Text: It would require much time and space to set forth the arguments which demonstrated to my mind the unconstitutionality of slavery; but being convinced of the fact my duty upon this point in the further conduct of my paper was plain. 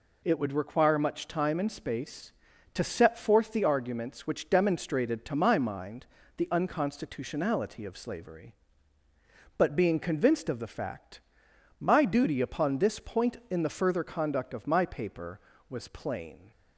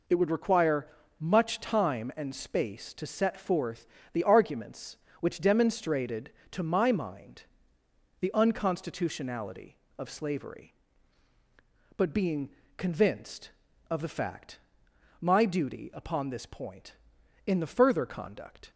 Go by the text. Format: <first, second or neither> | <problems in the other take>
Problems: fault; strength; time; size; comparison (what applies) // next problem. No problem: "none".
first | pauses between "require" and "much"; slight; at 0.8 s; 0.32 s long // pauses between "forth" and "the"; slight; at 3.8 s; 0.26 s long // pauses between "mind" and "the"; noticeable; at 7.4 s; 0.78 s long; slight in the first // pauses between "being" and "convinced"; slight; at 12.5 s; 0.26 s long // pauses between "fact" and "my"; noticeable; at 14.5 s; 0.62 s long; noticeable in the first // stops before "of my paper was plain"; at 18.7 s